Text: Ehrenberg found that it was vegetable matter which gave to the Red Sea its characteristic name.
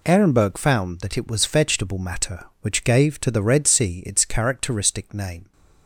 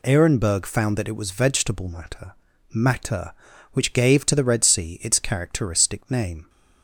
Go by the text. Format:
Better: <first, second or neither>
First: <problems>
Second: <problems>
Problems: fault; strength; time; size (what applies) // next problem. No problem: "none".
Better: first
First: none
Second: says "matter" twice; at 2.7 s